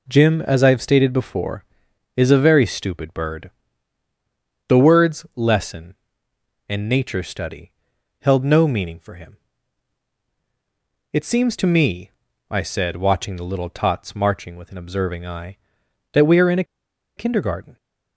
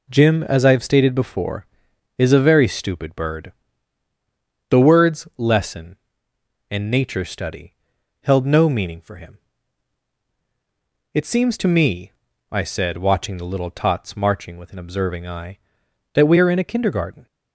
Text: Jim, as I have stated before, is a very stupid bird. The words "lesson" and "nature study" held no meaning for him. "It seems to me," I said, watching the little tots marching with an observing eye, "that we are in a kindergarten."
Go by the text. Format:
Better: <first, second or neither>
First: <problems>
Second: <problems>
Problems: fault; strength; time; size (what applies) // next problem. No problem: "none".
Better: second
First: pauses between "study" and "held"; noticeable; at 7.7 s; 0.48 s long // pauses between "a" and "kindergarten"; noticeable; at 16.6 s; 0.52 s long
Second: pauses between "study" and "held"; noticeable; at 7.7 s; 0.48 s long